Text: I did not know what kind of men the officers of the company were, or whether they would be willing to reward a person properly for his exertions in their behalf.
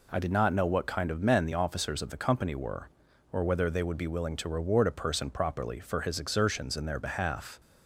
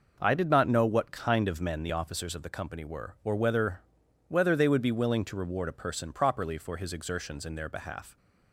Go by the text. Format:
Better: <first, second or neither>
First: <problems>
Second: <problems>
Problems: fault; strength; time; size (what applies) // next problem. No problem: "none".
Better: first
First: none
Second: says "whether" twice; at 4.2 s